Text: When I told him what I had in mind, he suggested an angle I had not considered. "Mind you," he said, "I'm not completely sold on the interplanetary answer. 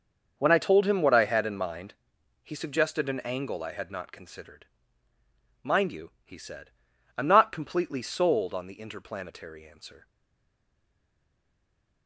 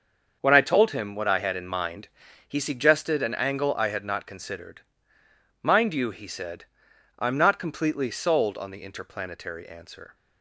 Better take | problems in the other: second | starts louder than the rest; noticeable; until 1.3 s; 6 dB; also in the second // stays silent after the last word; noticeable; from 10.0 s on; 2.0 s long

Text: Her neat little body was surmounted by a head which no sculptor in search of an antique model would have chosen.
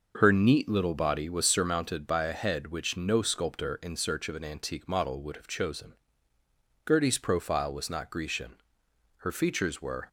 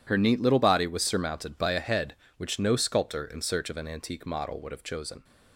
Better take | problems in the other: second | goes on to say "Gertie's profile was not Grecian her features were"; strong; from 6.8 s on; 3.2 s long

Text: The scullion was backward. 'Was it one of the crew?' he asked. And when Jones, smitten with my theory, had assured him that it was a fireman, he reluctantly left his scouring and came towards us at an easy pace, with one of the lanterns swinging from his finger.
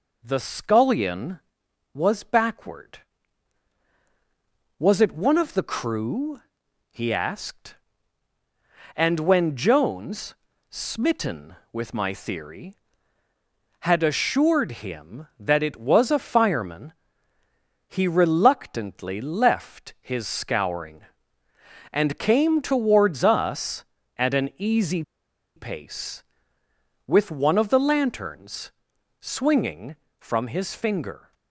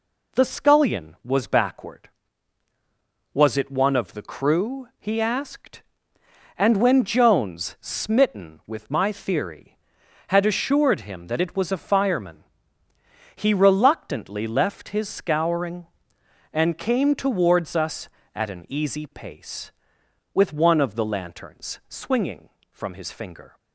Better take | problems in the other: second | pauses between "easy" and "pace"; noticeable; at 25.0 s; 0.54 s long // pauses between "lanterns" and "swinging"; noticeable; at 28.7 s; 0.48 s long

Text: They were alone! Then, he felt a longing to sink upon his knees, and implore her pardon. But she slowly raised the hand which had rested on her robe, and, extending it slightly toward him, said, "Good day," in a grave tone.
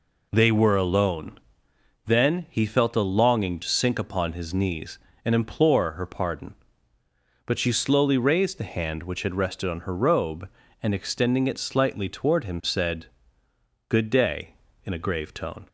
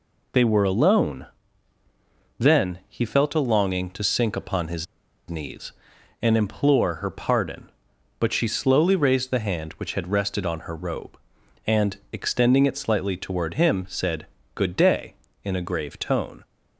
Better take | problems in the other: first | pauses between "his" and "knees"; at 4.8 s; 0.43 s long

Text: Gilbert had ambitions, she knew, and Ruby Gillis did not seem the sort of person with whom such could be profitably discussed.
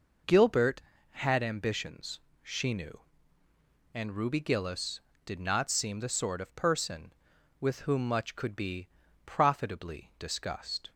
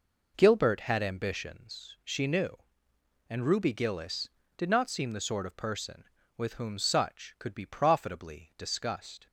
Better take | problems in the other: second | says "much" for "such"; at 8.0 s // pauses between "be" and "profitably"; at 8.8 s; 0.40 s long

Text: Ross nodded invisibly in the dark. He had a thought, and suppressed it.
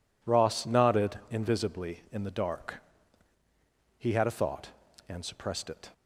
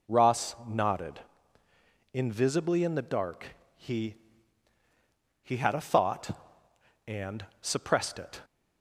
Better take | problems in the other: first | pauses between "nodded" and "invisibly"; noticeable; at 1.2 s; 0.92 s long // says "He" twice; at 5.4 s // pauses between "and" and "suppressed"; slight; at 7.4 s; 0.16 s long

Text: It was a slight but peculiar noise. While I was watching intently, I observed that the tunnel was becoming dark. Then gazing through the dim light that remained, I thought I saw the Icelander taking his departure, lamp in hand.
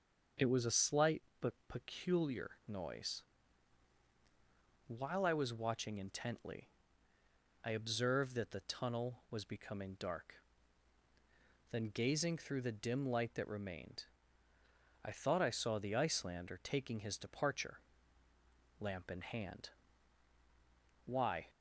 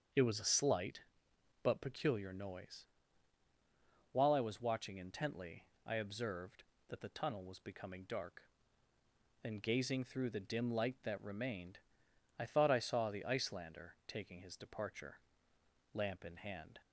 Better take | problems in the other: second | starts louder than the rest; until 1.7 s; 6.5 dB; also in the second // goes on to say "Why"; slight; from 21.0 s on; 0.44 s long

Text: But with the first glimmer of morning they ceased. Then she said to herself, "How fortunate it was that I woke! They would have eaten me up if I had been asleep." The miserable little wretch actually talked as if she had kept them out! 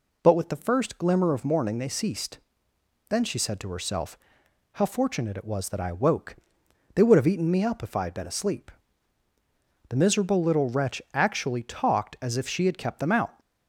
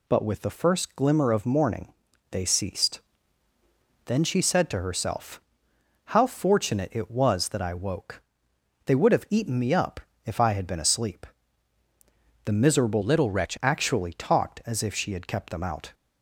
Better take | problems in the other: first | pauses between "morning" and "they"; at 1.9 s; 0.38 s long // pauses between "up" and "if"; slight; at 10.0 s; 0.24 s long // changes voice from "little" to "wretch"; from 13.0 to 13.5 s; 0.5 s long

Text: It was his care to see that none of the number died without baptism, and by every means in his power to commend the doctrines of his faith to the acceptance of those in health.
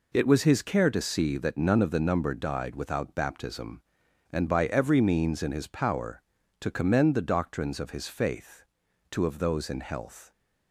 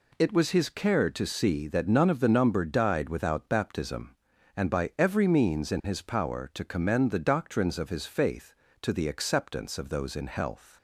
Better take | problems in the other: second | skips "the acceptance"; at 9.2 s

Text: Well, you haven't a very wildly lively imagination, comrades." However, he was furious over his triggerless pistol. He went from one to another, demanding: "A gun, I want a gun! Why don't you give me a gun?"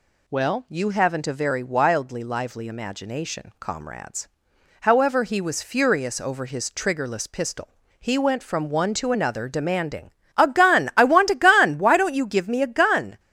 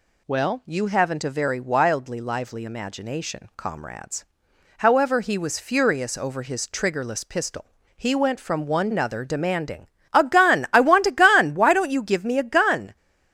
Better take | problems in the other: first | skips "to"; at 8.8 s

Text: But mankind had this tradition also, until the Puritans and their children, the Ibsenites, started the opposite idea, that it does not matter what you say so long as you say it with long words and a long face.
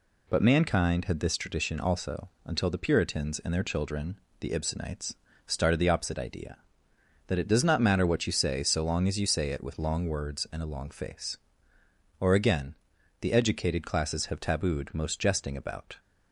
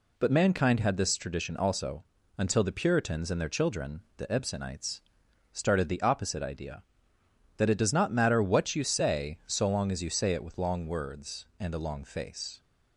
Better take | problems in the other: second | goes on to say "Or again the educated classes have tabooed most jesting about"; strong; from 12.1 s on; 3.7 s long

